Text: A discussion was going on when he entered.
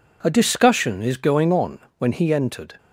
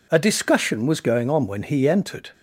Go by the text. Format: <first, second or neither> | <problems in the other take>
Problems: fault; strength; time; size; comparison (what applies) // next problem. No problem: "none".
second | says "is" for "was"; at 1.0 s // pauses between "on" and "when"; slight; at 1.7 s; 0.18 s long